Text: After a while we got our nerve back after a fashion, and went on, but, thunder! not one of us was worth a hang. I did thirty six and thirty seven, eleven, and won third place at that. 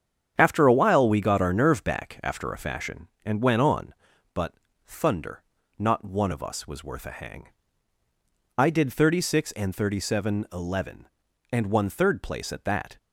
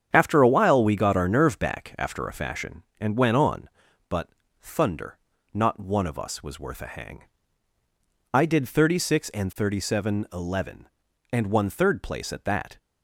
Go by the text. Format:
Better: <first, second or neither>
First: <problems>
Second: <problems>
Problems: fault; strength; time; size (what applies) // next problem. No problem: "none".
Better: neither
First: starts louder than the rest; strong; until 1.3 s; 8 dB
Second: starts louder than the rest; strong; until 1.1 s; 8 dB